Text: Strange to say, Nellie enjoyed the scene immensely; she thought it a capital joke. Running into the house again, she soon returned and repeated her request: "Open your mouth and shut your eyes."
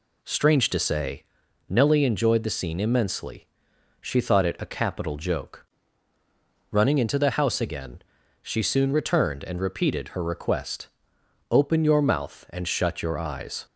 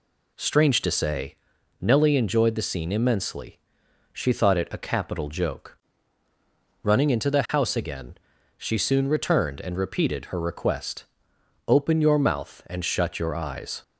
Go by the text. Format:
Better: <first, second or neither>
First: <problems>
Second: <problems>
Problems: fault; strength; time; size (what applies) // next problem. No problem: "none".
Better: neither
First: none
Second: none